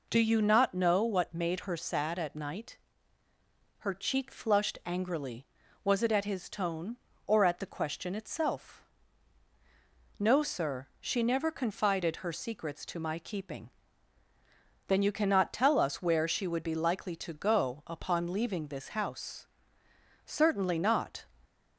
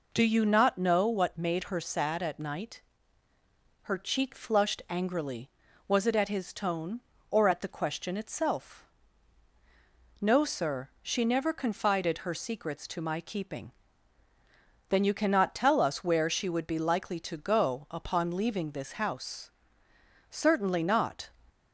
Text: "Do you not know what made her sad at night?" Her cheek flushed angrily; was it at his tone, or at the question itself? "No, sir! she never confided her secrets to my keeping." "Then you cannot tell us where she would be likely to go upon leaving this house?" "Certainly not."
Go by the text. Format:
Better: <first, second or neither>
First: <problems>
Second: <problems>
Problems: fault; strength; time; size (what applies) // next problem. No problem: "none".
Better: neither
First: none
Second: none